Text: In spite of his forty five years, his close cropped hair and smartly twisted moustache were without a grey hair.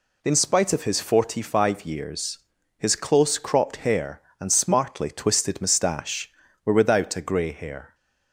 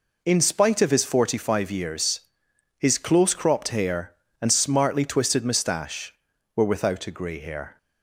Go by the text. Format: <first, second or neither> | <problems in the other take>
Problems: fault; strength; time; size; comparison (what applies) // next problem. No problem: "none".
neither | none